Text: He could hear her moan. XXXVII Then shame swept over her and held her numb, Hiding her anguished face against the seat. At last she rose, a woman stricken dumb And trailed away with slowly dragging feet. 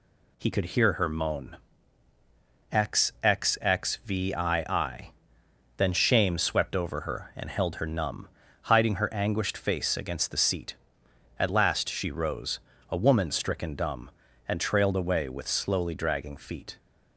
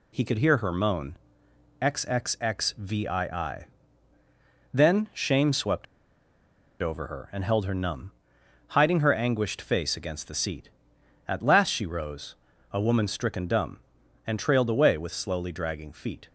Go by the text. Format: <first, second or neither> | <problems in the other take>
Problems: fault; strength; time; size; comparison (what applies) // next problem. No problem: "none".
first | pauses between "XXXVII" and "Then"; at 3.6 s; 1.0 s long; noticeable in the first // pauses between "swept" and "over"; noticeable; at 5.8 s; 0.97 s long